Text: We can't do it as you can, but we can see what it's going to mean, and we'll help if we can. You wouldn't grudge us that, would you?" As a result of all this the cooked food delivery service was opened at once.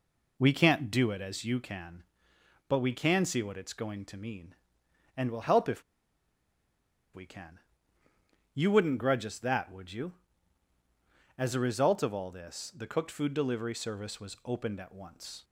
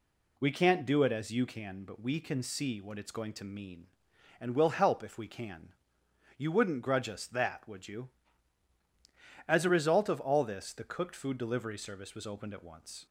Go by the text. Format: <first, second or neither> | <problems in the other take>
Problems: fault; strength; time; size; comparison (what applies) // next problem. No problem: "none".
second | pauses between "if" and "we"; strong; at 5.8 s; 1.3 s long